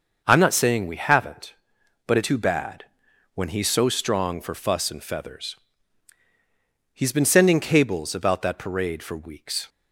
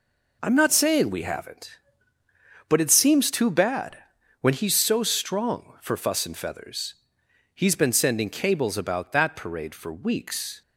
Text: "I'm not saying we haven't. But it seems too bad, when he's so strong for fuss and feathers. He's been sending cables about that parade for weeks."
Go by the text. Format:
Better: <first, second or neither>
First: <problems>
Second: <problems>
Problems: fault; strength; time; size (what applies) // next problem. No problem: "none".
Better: second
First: starts louder than the rest; until 1.2 s; 6.5 dB // skips "seems"; at 2.2 s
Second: none